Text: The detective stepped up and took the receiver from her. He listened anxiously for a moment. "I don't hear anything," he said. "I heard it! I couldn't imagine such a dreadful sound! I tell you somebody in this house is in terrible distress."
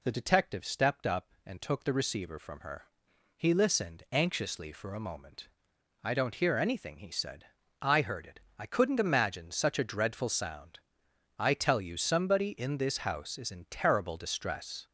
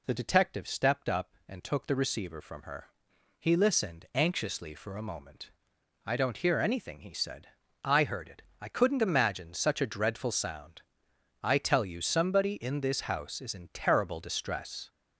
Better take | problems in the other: neither | none

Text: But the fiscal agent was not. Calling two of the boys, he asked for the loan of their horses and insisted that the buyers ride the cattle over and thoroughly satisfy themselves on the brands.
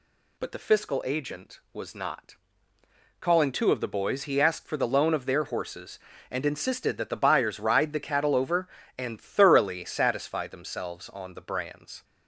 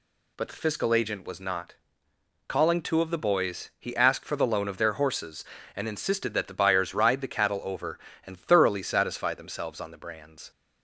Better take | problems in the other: neither | none

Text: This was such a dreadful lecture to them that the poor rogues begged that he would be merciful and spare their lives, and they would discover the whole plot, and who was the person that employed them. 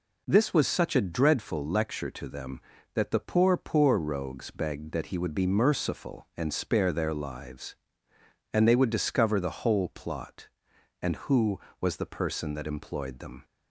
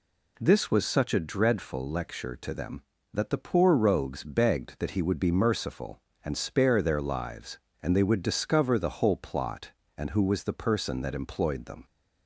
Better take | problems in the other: second | says "poor" twice; at 3.5 s

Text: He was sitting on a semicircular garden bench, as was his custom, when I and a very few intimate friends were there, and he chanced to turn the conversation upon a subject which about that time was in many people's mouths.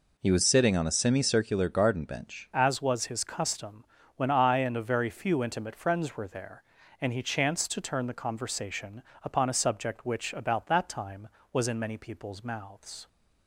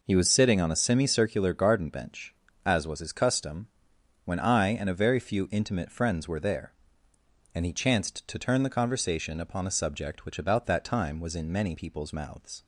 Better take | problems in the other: second | changes voice at "as"; from 2.5 s on; 10.5 s long // pauses between "conversation" and "upon"; slight; at 9.0 s; 0.22 s long

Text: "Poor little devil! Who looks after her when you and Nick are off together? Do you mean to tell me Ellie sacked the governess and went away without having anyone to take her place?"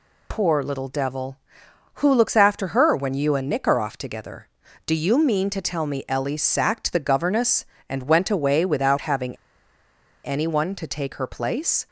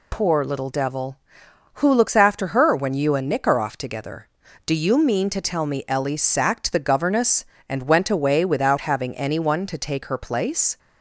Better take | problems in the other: second | pauses between "having" and "anyone"; noticeable; at 9.3 s; 0.88 s long

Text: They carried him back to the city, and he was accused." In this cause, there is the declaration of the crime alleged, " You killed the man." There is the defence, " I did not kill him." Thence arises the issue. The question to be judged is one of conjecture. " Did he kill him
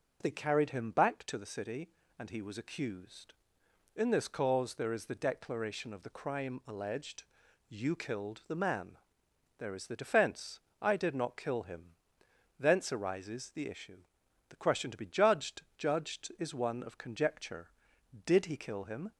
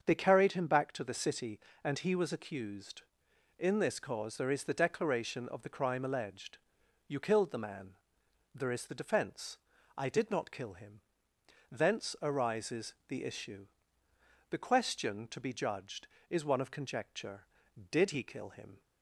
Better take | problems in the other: second | starts louder than the rest; until 1.2 s; 6.5 dB; strong in the second // says "judged" twice; at 15.7 s

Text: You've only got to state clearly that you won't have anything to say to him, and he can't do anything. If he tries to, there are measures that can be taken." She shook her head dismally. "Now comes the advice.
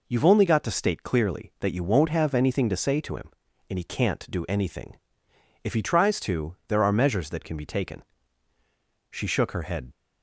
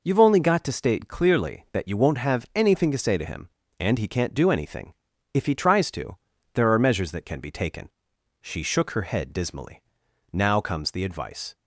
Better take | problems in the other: second | stops before "dismally Now comes the advice"; at 9.9 s

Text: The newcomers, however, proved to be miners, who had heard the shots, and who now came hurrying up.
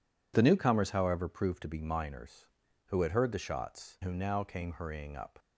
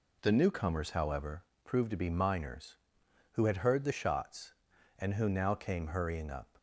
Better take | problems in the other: second | skips "and"; at 4.0 s

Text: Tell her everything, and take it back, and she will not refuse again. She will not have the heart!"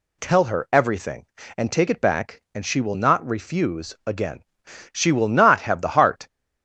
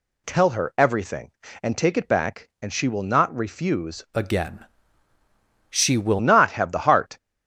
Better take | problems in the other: first | changes voice from "again" to "will"; from 4.1 to 6.2 s; 2.1 s long

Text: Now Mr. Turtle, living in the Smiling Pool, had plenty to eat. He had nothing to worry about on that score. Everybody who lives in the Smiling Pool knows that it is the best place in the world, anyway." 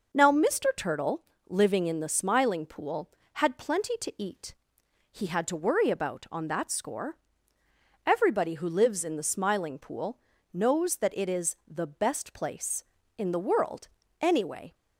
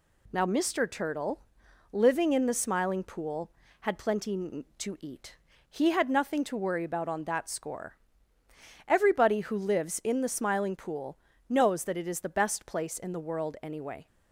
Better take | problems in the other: second | skips "nothing"; at 5.4 s // pauses between "Pool" and "knows"; slight; at 10.1 s; 0.34 s long; slight in the second

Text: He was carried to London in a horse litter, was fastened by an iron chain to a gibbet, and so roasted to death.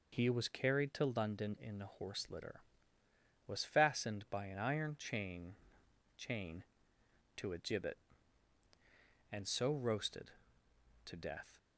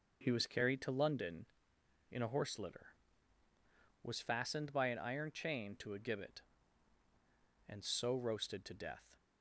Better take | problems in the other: second | says "chain" twice; at 6.1 s

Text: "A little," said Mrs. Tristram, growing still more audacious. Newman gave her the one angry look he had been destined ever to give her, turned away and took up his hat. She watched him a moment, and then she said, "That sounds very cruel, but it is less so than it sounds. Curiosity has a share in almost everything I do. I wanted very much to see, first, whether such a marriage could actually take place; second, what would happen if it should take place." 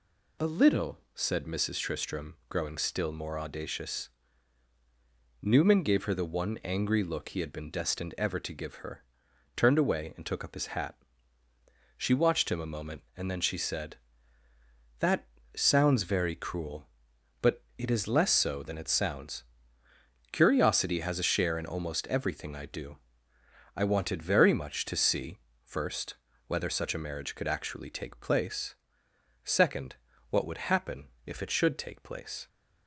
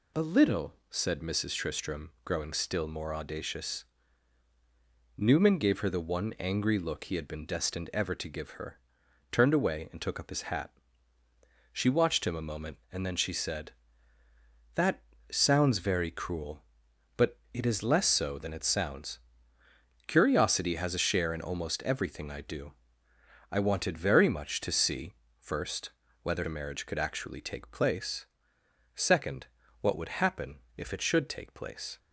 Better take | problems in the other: first | pauses between "That" and "sounds"; slight; at 15.0 s; 0.26 s long; slight in the first // pauses between "but" and "it"; slight; at 17.3 s; 0.16 s long; slight in the first // skips "such"; at 26.4 s // pauses between "happen" and "if"; slight; at 30.6 s; 0.16 s long; slight in the first

